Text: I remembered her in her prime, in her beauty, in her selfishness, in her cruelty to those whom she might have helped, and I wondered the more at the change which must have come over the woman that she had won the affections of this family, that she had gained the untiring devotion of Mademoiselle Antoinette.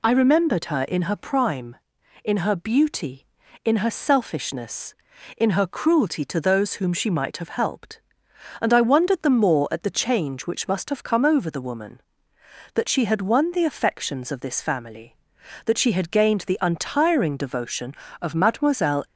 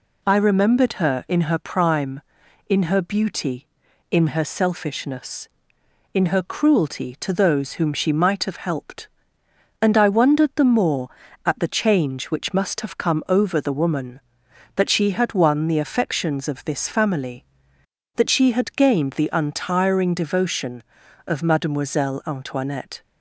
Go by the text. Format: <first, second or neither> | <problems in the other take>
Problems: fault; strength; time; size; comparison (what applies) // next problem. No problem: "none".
second | stops before "Antoinette"; at 19.0 s